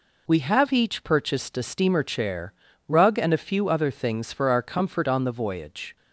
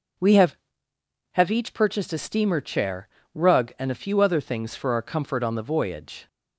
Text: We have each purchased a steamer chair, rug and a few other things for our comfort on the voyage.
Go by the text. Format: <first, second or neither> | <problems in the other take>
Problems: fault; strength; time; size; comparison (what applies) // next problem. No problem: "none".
first | starts louder than the rest; until 1.9 s; 6.5 dB // says "have" twice; at 1.3 s